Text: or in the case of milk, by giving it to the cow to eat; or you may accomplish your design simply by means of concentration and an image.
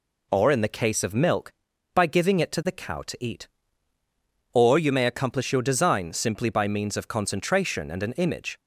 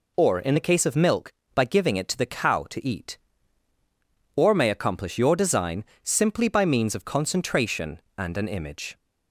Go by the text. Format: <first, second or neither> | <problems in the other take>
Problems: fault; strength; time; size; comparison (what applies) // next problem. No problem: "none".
first | skips "you"; at 4.5 s // pauses between "design" and "simply"; slight; at 5.8 s; 0.18 s long